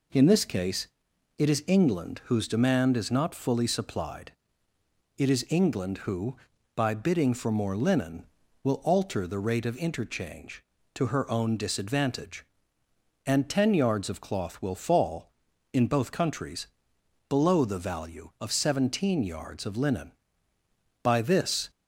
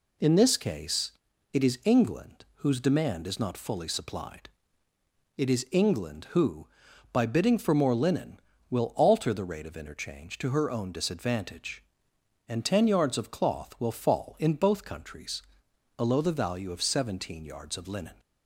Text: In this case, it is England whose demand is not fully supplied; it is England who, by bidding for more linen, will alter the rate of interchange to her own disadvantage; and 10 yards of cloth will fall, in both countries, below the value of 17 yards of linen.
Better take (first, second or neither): second